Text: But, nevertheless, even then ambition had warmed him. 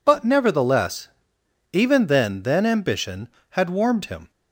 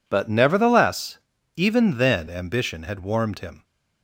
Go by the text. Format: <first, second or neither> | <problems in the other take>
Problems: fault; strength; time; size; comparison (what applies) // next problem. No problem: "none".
second | says "then" twice; at 2.4 s